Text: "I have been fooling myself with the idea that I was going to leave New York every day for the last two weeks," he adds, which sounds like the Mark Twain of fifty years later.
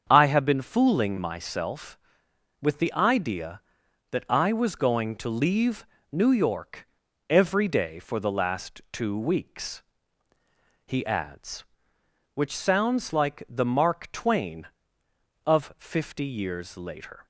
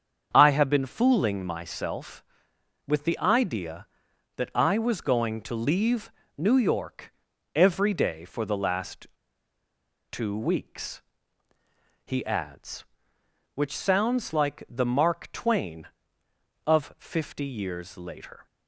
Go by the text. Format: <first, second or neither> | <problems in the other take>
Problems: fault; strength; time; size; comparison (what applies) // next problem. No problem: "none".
first | starts louder than the rest; strong; until 1.3 s; 7 dB; strong in the first // pauses between "leave" and "New"; slight; at 6.0 s; 0.28 s long; slight in the first // pauses between "York" and "every"; at 7.1 s; 0.42 s long; also in the first // pauses between "last" and "two"; at 9.0 s; 1.0 s long